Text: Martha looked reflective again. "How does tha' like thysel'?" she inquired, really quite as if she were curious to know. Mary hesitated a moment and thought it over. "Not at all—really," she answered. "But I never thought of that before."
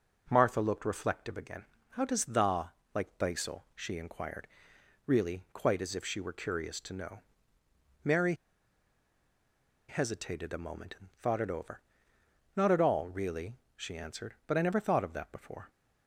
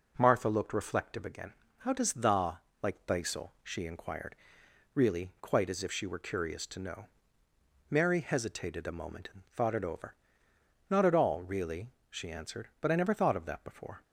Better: second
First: pauses between "tha" and "like"; slight; at 2.7 s; 0.20 s long // pauses between "Mary" and "hesitated"; strong; at 8.3 s; 1.5 s long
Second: pauses between "tha" and "like"; slight; at 2.6 s; 0.20 s long

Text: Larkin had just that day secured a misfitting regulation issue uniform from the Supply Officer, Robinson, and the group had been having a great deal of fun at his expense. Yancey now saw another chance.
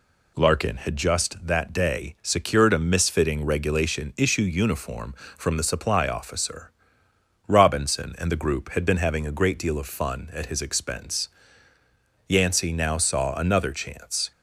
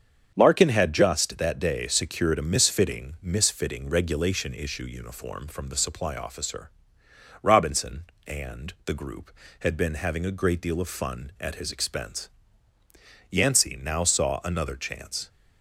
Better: first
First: none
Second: starts louder than the rest; strong; until 1.3 s; 7 dB // says "misfitting" twice; at 3.2 s

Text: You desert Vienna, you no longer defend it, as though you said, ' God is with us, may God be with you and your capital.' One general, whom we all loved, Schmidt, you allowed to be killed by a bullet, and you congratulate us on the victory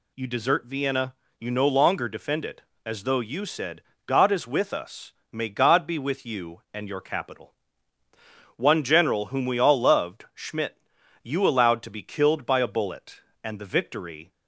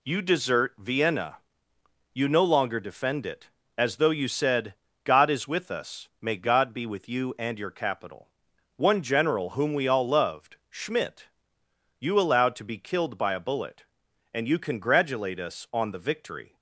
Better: second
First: skips "you congratulate us on"; at 13.5 s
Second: none

